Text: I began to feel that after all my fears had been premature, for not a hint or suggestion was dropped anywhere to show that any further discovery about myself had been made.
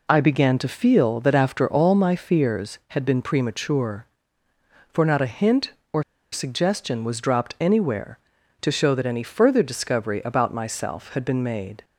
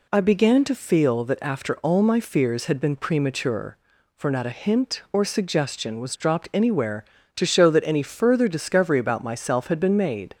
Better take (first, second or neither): second